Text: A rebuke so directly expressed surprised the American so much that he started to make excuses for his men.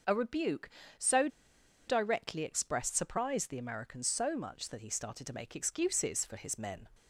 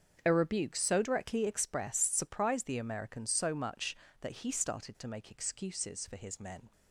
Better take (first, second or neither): second